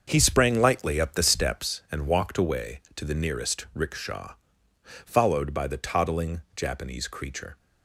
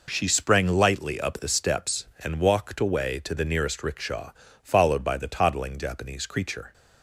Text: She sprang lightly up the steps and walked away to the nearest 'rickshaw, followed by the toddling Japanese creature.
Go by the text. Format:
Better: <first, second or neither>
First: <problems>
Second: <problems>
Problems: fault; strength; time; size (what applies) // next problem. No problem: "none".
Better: second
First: starts louder than the rest; until 1.0 s; 6.5 dB // says "He" for "She"; at 0.0 s // pauses between "toddling" and "Japanese"; slight; at 6.4 s; 0.16 s long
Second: none